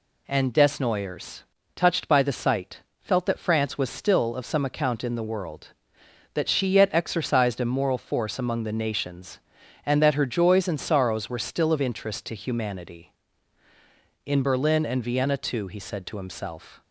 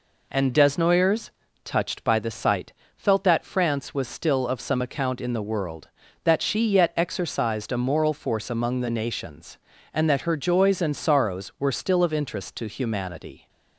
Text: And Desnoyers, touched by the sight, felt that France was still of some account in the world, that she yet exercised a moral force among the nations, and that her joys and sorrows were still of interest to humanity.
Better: second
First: goes on to say "In Berlin and Vienna too he said to himself"; strong; from 14.2 s on; 2.5 s long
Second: none

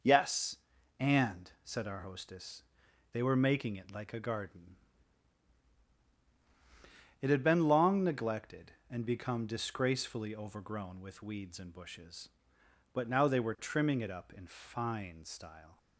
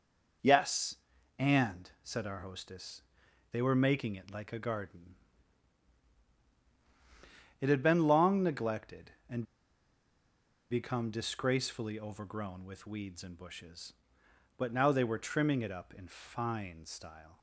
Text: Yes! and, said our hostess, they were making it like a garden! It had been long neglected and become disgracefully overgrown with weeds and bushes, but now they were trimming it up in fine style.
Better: first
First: none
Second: pauses between "and" and "become"; strong; at 9.4 s; 1.2 s long

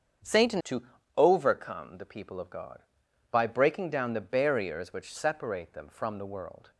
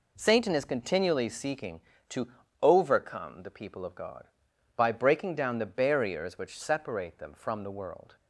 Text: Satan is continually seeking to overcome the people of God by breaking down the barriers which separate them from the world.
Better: second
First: starts louder than the rest; strong; until 1.5 s; 8 dB // skips "is continually seeking"; at 0.6 s // pauses between "to" and "overcome"; slight; at 0.8 s; 0.34 s long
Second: pauses between "to" and "overcome"; slight; at 2.2 s; 0.34 s long

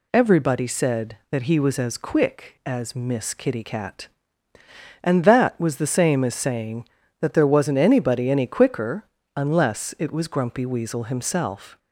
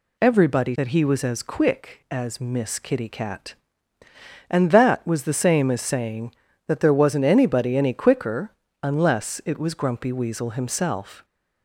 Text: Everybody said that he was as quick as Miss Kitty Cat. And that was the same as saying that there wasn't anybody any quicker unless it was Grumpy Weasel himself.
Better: first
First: pauses between "quicker" and "unless"; slight; at 9.0 s; 0.32 s long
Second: skips "said"; at 0.7 s // pauses between "quicker" and "unless"; slight; at 8.5 s; 0.32 s long

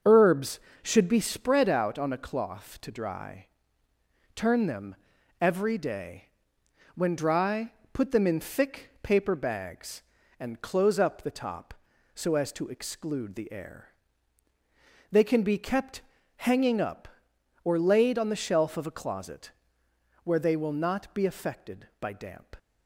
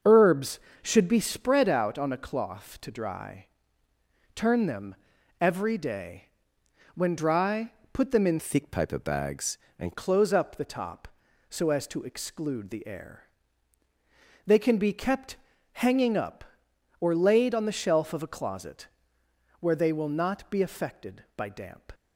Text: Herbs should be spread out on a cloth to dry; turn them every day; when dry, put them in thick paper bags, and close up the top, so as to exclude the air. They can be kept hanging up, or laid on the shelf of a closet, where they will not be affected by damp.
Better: first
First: starts louder than the rest; until 1.2 s; 6 dB // pauses between "them" and "every"; at 4.9 s; 0.44 s long // pauses between "kept" and "hanging"; at 16.0 s; 0.36 s long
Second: starts louder than the rest; until 1.2 s; 6.5 dB // pauses between "them" and "every"; at 4.9 s; 0.44 s long // changes voice from "thick" to "and"; from 8.3 to 9.9 s; 1.6 s long // pauses between "kept" and "hanging"; at 15.3 s; 0.38 s long

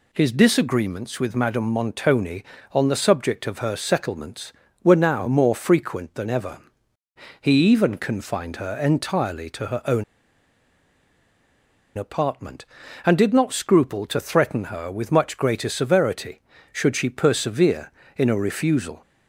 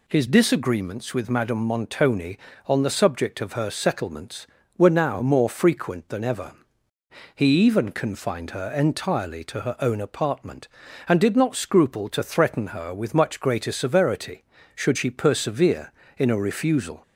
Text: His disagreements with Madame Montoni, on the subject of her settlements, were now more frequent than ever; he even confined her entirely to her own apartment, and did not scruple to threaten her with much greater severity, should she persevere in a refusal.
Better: second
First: pauses between "own" and "apartment"; strong; at 10.0 s; 1.9 s long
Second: none

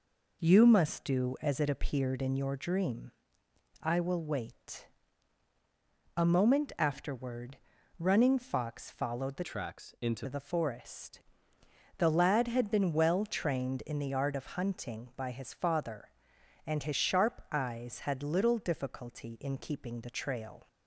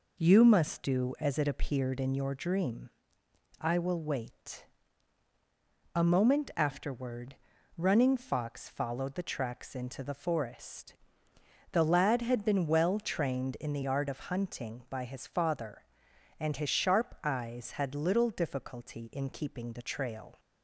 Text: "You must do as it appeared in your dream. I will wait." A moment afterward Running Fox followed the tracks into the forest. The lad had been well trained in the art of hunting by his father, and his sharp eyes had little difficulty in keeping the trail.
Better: second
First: pauses between "afterward" and "Running"; at 7.5 s; 0.42 s long // changes voice from "tracks" to "into"; from 9.4 to 10.2 s; 0.8 s long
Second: pauses between "afterward" and "Running"; at 7.3 s; 0.42 s long

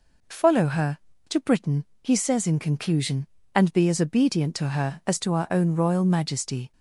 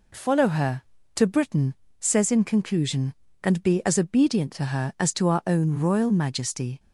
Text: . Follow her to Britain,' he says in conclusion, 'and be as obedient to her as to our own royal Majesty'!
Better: first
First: none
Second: skips "he"; at 1.8 s

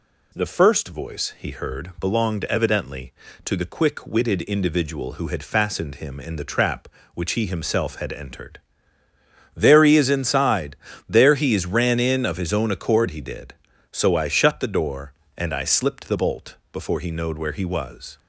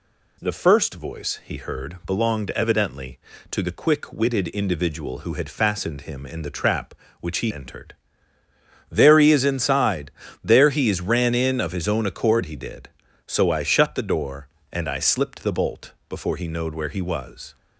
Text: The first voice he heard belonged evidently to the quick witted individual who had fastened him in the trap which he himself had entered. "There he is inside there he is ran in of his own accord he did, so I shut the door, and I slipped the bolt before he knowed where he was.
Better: first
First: pauses between "inside" and "there"; slight; at 10.7 s; 0.30 s long // pauses between "bolt" and "before"; slight; at 16.5 s; 0.16 s long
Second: skips "himself had"; at 7.5 s // pauses between "inside" and "there"; slight; at 10.1 s; 0.30 s long // pauses between "bolt" and "before"; slight; at 15.9 s; 0.16 s long

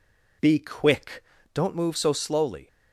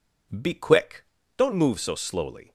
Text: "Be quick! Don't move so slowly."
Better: neither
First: none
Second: none

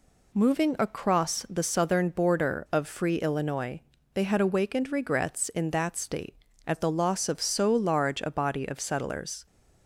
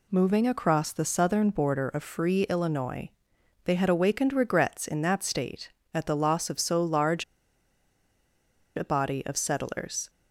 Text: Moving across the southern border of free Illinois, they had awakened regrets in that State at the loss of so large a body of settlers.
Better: first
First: none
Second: pauses between "large" and "a"; strong; at 7.2 s; 1.5 s long

